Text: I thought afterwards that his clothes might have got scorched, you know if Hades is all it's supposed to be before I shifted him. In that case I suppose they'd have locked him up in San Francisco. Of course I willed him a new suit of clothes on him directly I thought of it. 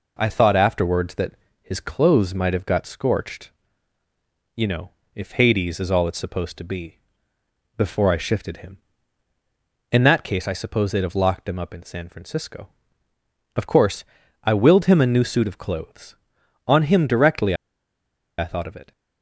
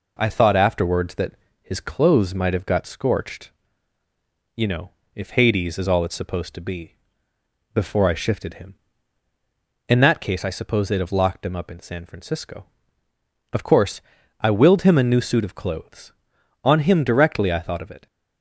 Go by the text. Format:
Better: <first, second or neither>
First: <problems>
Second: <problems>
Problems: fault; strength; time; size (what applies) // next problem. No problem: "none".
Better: second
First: pauses between "that" and "his"; slight; at 1.3 s; 0.28 s long // pauses between "know" and "if"; slight; at 4.8 s; 0.24 s long // pauses between "be" and "before"; noticeable; at 6.9 s; 0.76 s long // pauses between "course" and "I"; at 14.0 s; 0.40 s long // pauses between "directly" and "I"; noticeable; at 17.5 s; 0.82 s long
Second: pauses between "that" and "his"; slight; at 1.3 s; 0.28 s long // pauses between "know" and "if"; slight; at 4.8 s; 0.24 s long // pauses between "be" and "before"; noticeable; at 6.9 s; 0.76 s long // pauses between "course" and "I"; at 14.0 s; 0.40 s long